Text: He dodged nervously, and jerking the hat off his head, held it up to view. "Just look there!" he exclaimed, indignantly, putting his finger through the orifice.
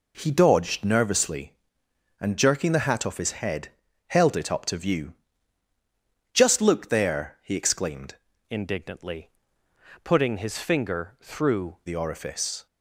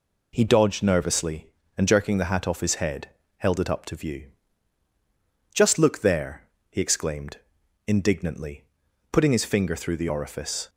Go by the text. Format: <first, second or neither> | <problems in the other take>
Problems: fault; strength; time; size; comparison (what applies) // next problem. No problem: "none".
second | changes voice from "indignantly" to "through"; from 8.4 to 11.7 s; 3.3 s long